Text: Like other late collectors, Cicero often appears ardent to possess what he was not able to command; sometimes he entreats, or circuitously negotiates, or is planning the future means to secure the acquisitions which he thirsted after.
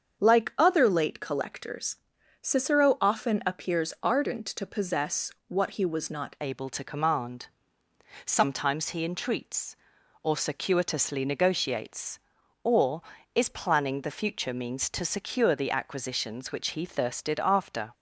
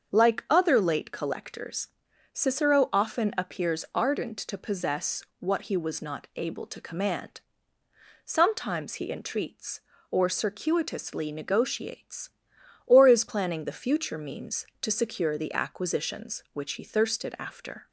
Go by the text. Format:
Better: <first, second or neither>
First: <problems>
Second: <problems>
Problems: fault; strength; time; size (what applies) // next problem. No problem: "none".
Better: second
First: starts louder than the rest; strong; until 1.2 s; 7 dB // pauses between "possess" and "what"; slight; at 5.3 s; 0.18 s long // changes voice at "able"; from 6.3 s on; 11.6 s long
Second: starts louder than the rest; until 1.1 s; 7 dB // pauses between "possess" and "what"; slight; at 5.2 s; 0.18 s long